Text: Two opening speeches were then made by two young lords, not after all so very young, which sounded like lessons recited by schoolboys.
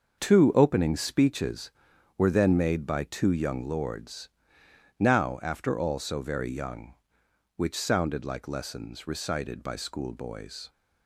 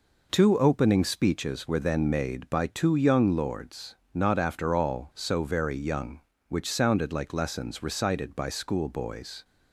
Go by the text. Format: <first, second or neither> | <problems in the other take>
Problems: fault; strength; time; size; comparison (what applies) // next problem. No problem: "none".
second | starts louder than the rest; until 1.2 s; 6.5 dB // says "now" for "not"; at 4.9 s